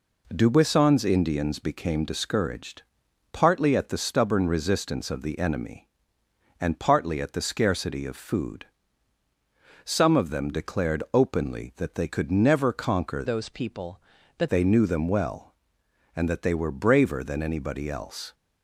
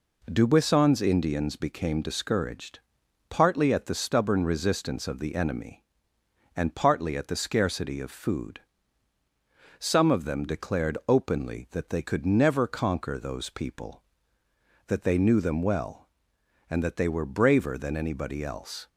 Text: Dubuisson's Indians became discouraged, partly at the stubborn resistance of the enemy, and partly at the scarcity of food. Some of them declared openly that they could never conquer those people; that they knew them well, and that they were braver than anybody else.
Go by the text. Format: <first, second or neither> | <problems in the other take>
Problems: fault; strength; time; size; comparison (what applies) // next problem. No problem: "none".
second | changes voice from "those" to "that"; from 13.2 to 14.4 s; 1.2 s long